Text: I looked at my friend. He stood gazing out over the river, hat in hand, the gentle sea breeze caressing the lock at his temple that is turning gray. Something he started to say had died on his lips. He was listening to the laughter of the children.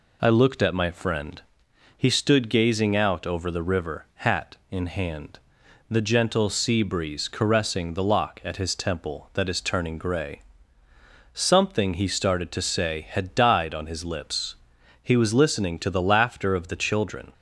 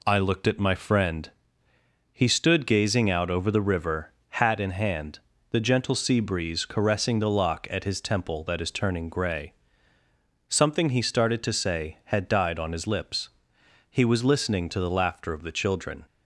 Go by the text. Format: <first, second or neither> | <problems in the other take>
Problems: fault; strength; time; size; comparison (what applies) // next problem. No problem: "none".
neither | none